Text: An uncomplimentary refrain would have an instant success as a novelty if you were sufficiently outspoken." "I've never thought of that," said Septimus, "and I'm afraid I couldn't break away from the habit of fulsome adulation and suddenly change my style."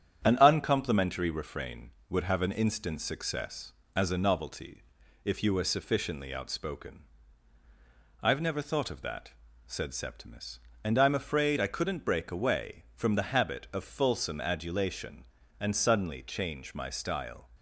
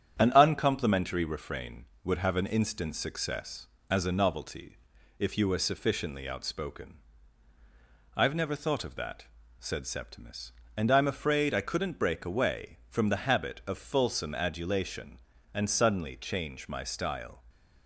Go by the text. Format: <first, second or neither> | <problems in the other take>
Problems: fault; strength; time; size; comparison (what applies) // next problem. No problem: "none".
neither | starts louder than the rest; strong; the same in both // pauses between "novelty" and "if"; the same in both